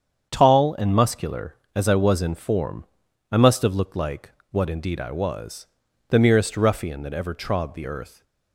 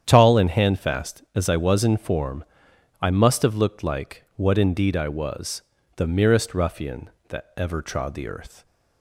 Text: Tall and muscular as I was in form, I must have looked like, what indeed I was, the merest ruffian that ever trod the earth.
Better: first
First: starts louder than the rest; strong; until 1.3 s; 8 dB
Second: starts louder than the rest; strong; until 1.0 s; 9 dB // says "handfast" for "muscular"; at 0.5 s

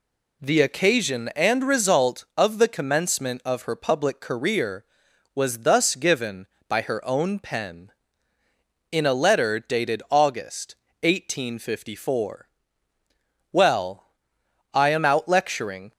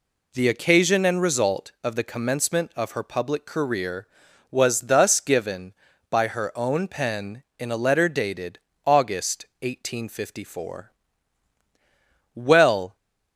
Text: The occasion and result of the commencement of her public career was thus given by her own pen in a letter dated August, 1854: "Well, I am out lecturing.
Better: first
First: none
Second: pauses between "dated" and "August"; slight; at 8.5 s; 0.26 s long // stops before "I am out lecturing"; at 12.9 s

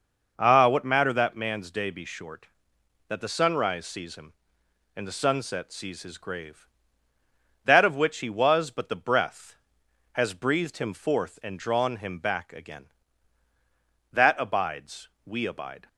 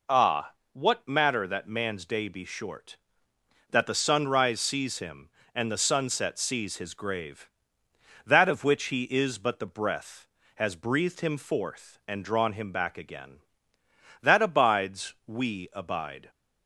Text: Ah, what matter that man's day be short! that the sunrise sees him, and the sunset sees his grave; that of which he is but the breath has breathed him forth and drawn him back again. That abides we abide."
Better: second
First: says "was" for "is"; at 8.2 s // pauses between "abides" and "we"; slight; at 15.0 s; 0.16 s long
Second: none

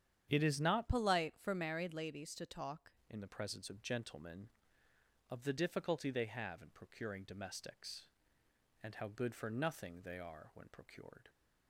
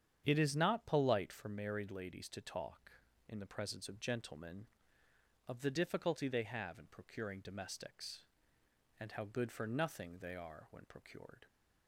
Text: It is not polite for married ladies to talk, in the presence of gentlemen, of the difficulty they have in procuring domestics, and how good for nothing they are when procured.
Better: second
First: starts louder than the rest; strong; until 1.2 s; 9 dB // changes voice from "polite" to "talk"; from 0.8 to 2.9 s; 2.1 s long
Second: starts louder than the rest; strong; until 1.2 s; 8.5 dB

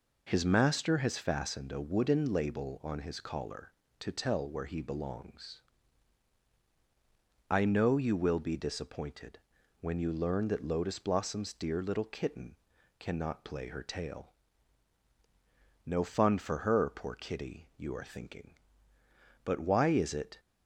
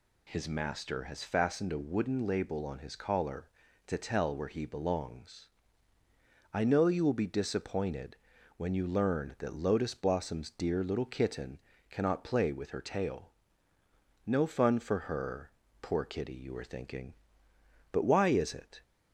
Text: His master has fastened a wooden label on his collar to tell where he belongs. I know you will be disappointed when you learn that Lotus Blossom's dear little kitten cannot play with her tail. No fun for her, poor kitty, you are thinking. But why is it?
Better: second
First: pauses between "disappointed" and "when"; at 9.3 s; 0.42 s long // pauses between "kitten" and "cannot"; at 12.5 s; 0.44 s long // skips "with"; at 13.6 s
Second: pauses between "disappointed" and "when"; at 8.1 s; 0.40 s long // pauses between "kitten" and "cannot"; slight; at 11.5 s; 0.30 s long

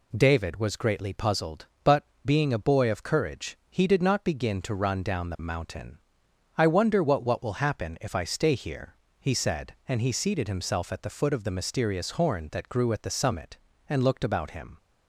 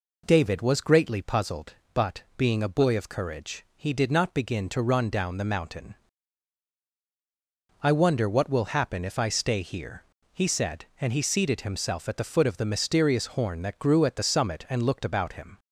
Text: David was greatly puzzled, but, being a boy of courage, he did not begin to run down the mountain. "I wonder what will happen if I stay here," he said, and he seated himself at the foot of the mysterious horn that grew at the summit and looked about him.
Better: second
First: says "what" twice; at 7.2 s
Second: none

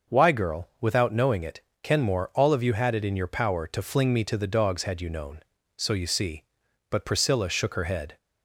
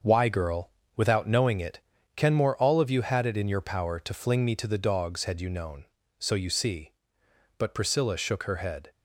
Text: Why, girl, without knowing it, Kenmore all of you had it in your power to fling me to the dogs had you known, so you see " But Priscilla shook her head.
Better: first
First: starts louder than the rest; until 1.2 s; 6.5 dB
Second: gets quieter; strong; throughout; 11.5 dB // starts louder than the rest; until 1.2 s; 6.5 dB

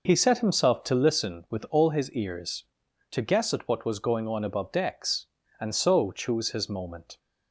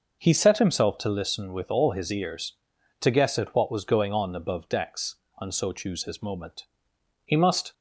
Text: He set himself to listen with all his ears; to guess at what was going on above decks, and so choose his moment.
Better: first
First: none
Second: goes on to say "He must"; slight; from 7.2 s on; 0.48 s long

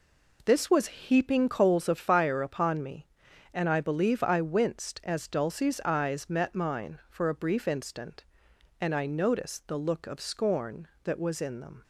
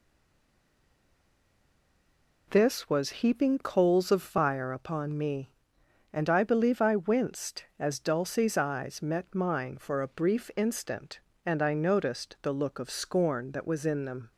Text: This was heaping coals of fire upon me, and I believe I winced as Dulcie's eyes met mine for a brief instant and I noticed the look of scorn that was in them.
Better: first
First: none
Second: stays silent before the first word; until 2.4 s; 2.4 s long

